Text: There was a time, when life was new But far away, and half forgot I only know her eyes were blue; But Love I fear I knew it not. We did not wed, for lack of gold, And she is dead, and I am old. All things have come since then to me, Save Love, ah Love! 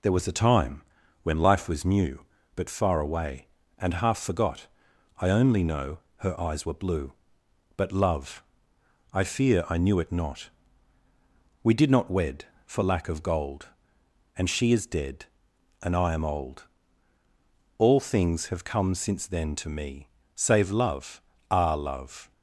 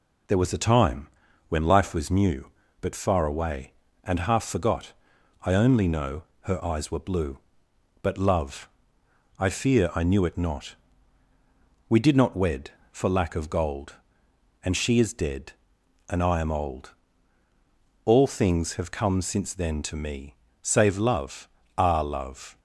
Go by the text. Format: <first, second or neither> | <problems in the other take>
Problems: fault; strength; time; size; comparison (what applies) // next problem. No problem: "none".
neither | pauses between "forgot" and "I"; noticeable; the same in both // pauses between "know" and "her"; slight; the same in both // pauses between "Love" and "I"; noticeable; the same in both